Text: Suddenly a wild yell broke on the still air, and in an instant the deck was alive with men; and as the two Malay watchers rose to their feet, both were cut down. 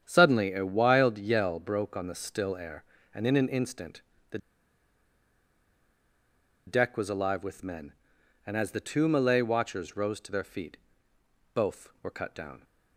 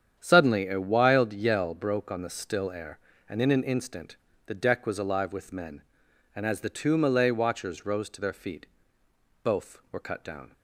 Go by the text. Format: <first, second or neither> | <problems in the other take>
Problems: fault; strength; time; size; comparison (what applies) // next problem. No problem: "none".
second | starts louder than the rest; strong; until 1.0 s; 8.5 dB; strong in the second // pauses between "instant" and "the"; slight; at 4.0 s; 0.30 s long; slight in the second // pauses between "the" and "deck"; strong; at 4.3 s; 2.2 s long